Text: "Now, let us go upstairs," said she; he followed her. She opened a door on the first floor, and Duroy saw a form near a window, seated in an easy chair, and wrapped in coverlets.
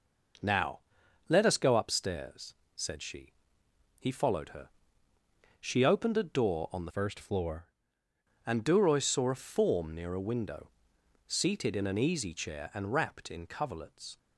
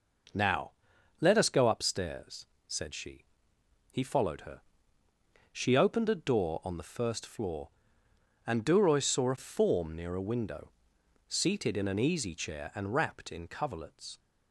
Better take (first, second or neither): second